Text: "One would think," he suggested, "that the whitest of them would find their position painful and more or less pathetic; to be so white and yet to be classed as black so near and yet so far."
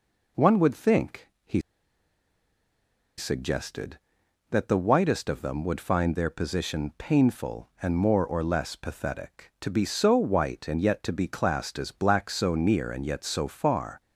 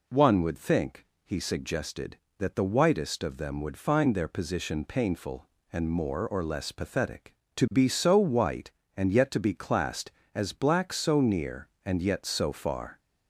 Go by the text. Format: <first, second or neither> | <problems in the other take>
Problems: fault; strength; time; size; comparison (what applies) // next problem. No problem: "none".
second | pauses between "he" and "suggested"; strong; at 1.6 s; 1.5 s long